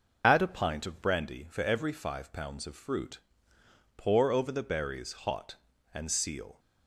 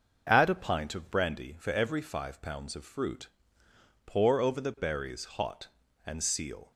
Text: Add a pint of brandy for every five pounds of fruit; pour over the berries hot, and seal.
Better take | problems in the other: second | loses the start of "Add"; at 0.2 s; 55 ms

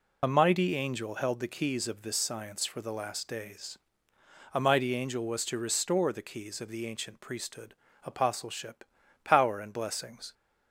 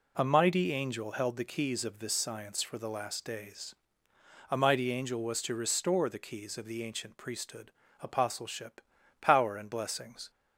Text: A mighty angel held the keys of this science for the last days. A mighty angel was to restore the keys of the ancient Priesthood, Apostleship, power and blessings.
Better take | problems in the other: second | loses the start of "A"; at 0.2 s; 40 ms

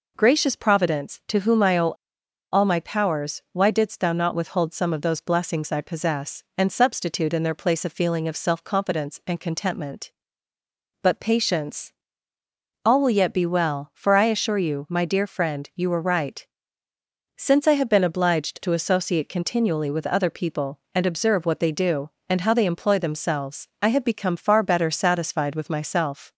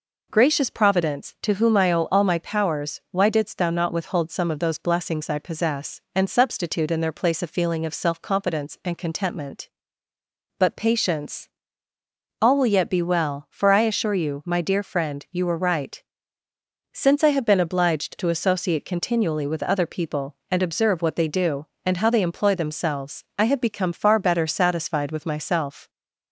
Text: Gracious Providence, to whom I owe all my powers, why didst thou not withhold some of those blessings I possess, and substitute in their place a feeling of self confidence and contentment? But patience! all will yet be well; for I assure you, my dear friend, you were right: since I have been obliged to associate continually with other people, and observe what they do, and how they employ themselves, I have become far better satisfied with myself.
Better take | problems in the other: second | pauses between "owe" and "all"; noticeable; at 1.9 s; 0.57 s long

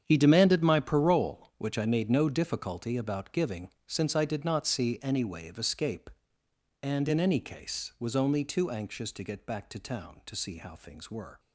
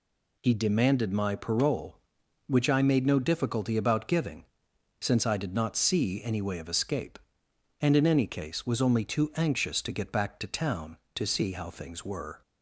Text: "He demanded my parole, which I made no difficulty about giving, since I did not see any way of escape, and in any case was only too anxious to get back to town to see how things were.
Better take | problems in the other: second | gets quieter; strong; throughout; 12.5 dB

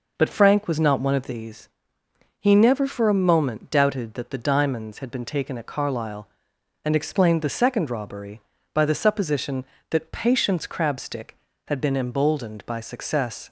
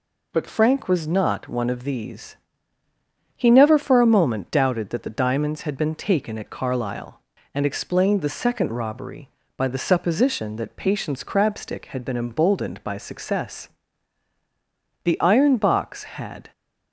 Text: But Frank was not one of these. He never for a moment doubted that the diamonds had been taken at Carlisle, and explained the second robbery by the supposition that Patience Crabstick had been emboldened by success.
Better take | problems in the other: first | goes on to say "The iron box had"; from 15.0 s on; 1.4 s long

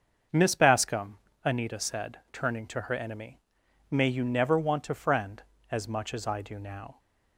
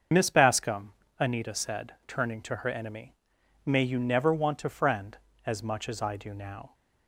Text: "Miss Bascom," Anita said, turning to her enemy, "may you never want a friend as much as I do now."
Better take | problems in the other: first | loses the start of "Miss"; at 0.1 s; 55 ms // starts louder than the rest; until 1.3 s; 6.5 dB; also in the first

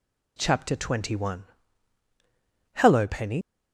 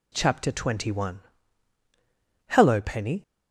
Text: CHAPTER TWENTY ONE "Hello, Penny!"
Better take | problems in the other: second | pauses between "ONE" and "Hello"; strong; at 1.4 s; 1.3 s long; strong in the second // leaves "Penny" unfinished; at 3.4 s; 60 ms

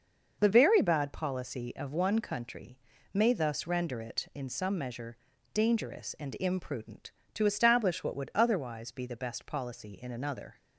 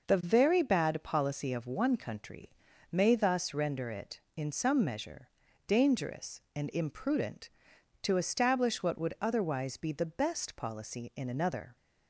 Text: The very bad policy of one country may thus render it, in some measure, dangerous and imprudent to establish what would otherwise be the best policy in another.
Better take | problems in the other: neither | pauses between "country" and "may"; the same in both

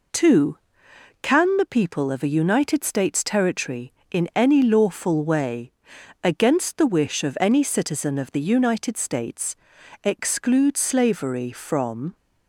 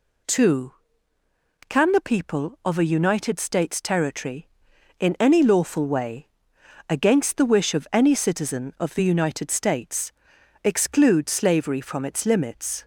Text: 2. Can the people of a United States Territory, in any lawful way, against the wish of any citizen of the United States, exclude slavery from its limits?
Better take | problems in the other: second | stops before "its limits"; at 12.1 s

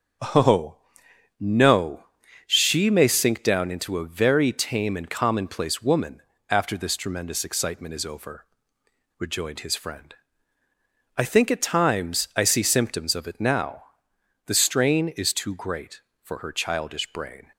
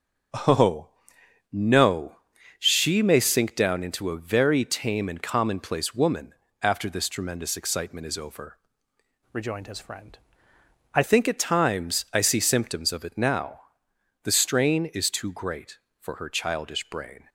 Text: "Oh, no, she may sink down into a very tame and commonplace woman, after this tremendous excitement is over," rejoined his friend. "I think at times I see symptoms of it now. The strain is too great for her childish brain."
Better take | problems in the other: first | starts louder than the rest; until 1.9 s; 6 dB; strong in the first // changes voice from "rejoined" to "I"; from 9.3 to 11.0 s; 1.7 s long

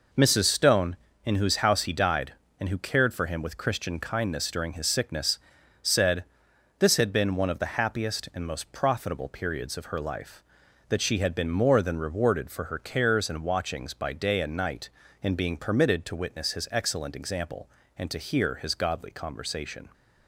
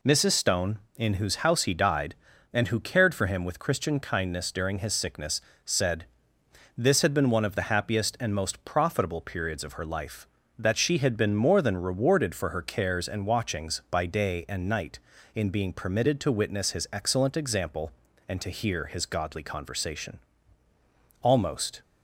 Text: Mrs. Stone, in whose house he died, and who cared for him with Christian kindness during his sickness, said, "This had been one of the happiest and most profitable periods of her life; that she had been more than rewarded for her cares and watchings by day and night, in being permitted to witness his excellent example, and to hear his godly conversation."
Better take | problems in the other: first | goes on to say "Almost"; from 21.2 s on; 0.60 s long

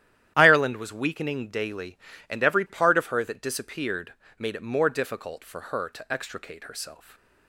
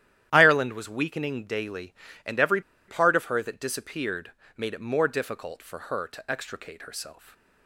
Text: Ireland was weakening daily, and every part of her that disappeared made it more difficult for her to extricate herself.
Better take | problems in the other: first | starts louder than the rest; strong; until 1.3 s; 11.5 dB; strong in the first // pauses between "every" and "part"; slight; at 2.5 s; 0.28 s long // pauses between "disappeared" and "made"; slight; at 4.3 s; 0.24 s long; slight in the first

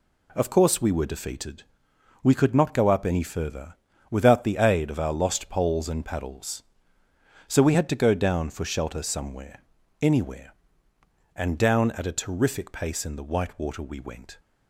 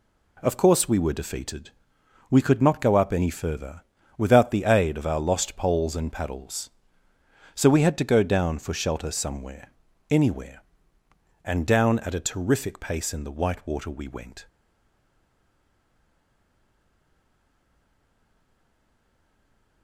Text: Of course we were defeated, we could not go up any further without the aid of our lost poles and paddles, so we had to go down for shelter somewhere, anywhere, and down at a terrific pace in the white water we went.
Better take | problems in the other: first | pauses between "further" and "without"; slight; at 3.8 s; 0.36 s long; slight in the first // stays silent after the last word; strong; from 14.4 s on; 5.4 s long

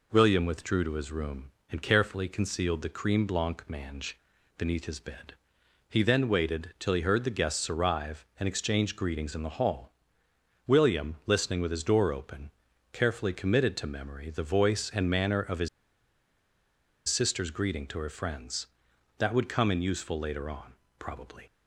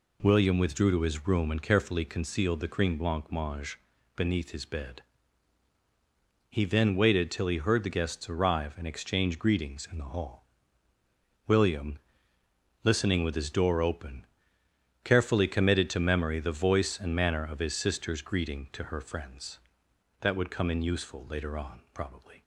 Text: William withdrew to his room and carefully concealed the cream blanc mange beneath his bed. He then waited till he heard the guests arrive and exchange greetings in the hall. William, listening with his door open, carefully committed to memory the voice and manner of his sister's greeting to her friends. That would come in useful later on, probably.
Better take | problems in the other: second | pauses between "mange" and "beneath"; at 4.1 s; 0.40 s long; slight in the second // pauses between "his" and "sister's"; strong; at 15.6 s; 1.4 s long

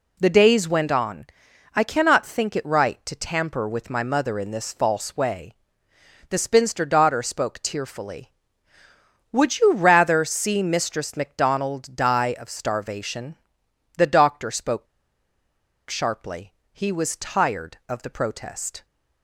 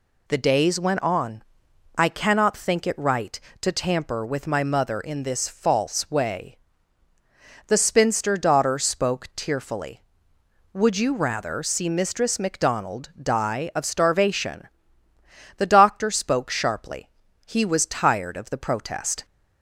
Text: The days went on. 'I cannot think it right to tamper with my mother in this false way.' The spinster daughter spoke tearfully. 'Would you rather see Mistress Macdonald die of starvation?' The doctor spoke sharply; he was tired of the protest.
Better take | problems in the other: second | pauses between "spoke" and "sharply"; at 14.8 s; 1.0 s long

